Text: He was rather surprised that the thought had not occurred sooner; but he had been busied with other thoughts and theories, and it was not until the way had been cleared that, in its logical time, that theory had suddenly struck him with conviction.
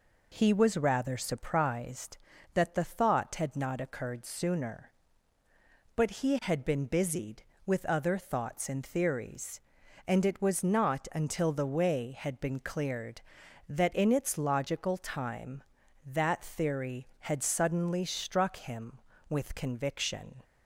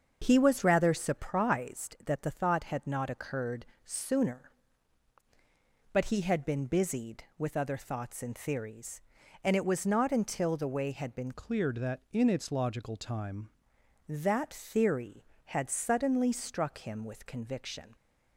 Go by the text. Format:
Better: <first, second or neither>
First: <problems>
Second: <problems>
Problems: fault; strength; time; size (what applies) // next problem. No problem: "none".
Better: first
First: none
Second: starts louder than the rest; until 1.2 s; 6.5 dB // pauses between "occurred" and "sooner"; slight; at 3.6 s; 0.20 s long // changes voice from "cleared" to "time"; from 11.3 to 13.4 s; 2.1 s long